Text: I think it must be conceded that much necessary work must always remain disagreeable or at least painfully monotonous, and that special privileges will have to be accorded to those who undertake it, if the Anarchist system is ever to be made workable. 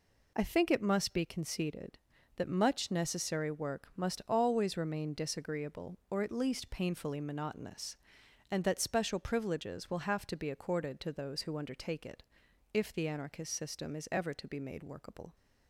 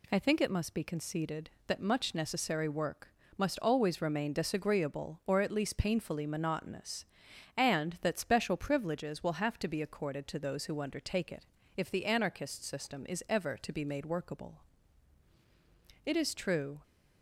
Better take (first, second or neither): first